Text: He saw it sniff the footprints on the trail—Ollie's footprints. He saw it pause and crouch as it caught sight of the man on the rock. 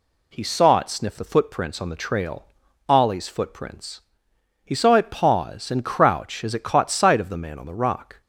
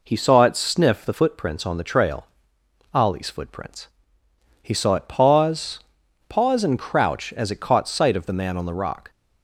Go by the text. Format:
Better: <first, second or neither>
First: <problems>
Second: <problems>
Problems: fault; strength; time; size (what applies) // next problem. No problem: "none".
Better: first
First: none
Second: says "pause" twice; at 6.2 s